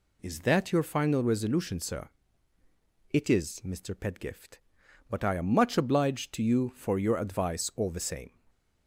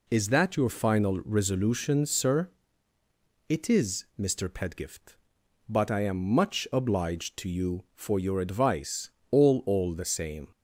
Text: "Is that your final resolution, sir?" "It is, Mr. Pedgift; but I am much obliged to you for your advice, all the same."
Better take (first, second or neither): first